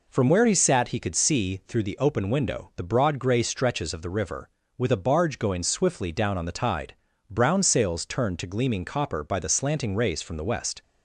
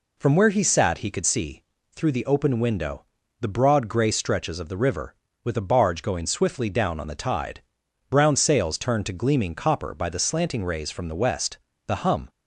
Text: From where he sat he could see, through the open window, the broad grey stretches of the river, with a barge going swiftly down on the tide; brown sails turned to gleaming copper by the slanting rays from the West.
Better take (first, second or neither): first